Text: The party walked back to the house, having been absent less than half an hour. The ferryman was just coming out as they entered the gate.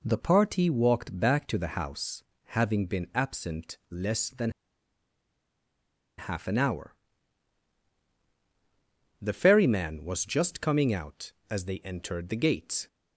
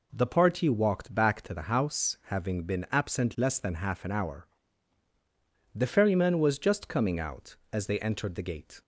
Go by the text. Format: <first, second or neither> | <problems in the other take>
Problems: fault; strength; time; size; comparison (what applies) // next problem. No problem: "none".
second | pauses between "than" and "half"; strong; at 4.4 s; 1.6 s long